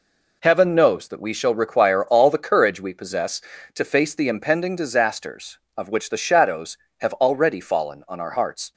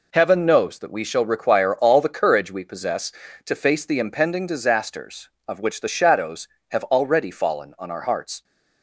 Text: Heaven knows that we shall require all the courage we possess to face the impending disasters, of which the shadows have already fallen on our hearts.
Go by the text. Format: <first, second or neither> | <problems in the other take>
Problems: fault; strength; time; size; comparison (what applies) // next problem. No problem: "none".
neither | none